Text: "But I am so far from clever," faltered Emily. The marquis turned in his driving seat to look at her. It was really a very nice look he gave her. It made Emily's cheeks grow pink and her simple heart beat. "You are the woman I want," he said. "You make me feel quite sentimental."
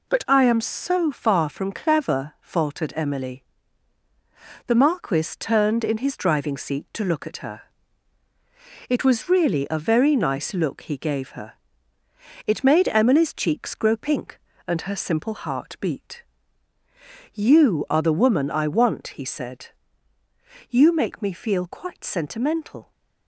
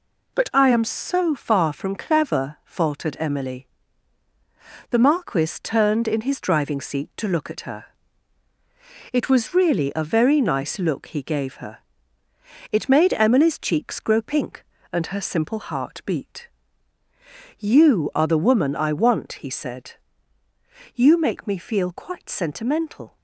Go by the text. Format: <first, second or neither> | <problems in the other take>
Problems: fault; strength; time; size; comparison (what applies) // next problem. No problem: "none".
neither | none